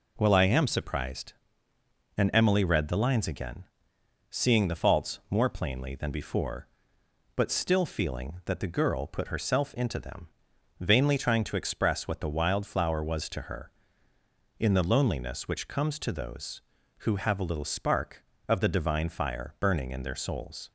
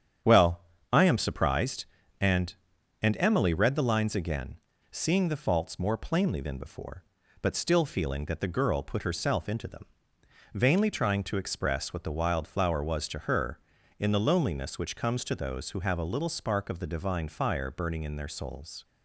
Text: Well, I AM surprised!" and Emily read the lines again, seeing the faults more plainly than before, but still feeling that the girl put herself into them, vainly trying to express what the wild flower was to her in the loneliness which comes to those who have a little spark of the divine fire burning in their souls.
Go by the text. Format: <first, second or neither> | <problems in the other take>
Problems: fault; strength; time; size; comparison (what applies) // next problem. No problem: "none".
first | starts louder than the rest; strong; until 1.5 s; 8.5 dB // says "and" twice; at 3.0 s